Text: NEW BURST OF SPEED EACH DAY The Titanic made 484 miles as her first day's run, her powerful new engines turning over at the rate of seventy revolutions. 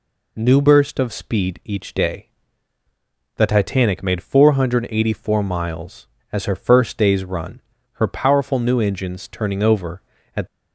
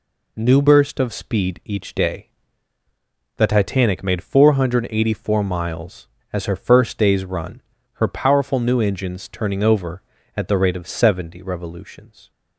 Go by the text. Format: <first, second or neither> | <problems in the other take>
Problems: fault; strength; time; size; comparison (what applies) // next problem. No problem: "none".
second | pauses between "DAY" and "The"; at 2.2 s; 1.0 s long; also in the second // stops before "the rate of seventy revolutions"; at 10.4 s